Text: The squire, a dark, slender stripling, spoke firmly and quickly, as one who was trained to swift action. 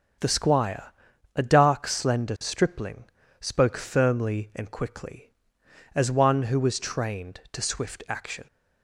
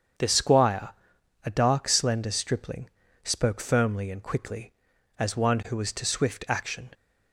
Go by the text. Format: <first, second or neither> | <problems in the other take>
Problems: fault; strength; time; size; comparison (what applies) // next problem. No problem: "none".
first | starts louder than the rest; strong; until 1.7 s; 7.5 dB; also in the first // skips "trained"; at 5.9 s